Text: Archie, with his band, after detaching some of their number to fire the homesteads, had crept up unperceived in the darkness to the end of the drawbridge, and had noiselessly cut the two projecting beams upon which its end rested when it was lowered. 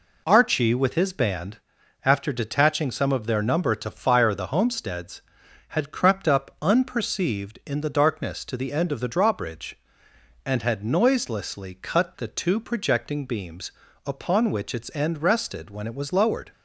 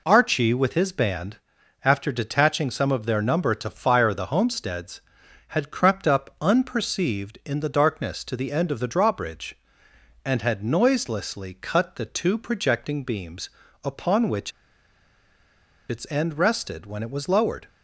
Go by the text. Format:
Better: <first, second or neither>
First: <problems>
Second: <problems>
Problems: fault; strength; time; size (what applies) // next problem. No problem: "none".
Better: first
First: pauses between "beams" and "upon"; slight; at 13.7 s; 0.34 s long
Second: pauses between "beams" and "upon"; slight; at 13.4 s; 0.34 s long // pauses between "which" and "its"; strong; at 14.5 s; 1.3 s long